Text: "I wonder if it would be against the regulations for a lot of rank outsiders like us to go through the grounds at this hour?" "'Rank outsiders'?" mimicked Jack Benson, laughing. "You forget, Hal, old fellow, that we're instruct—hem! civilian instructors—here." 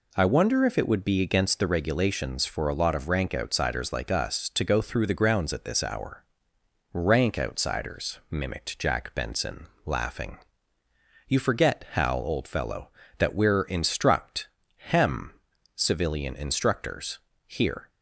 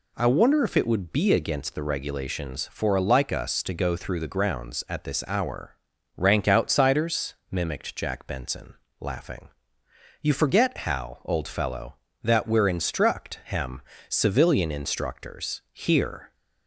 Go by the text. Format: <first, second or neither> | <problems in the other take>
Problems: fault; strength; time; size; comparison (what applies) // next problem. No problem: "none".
first | skips "lot of rank outsiders"; at 3.0 s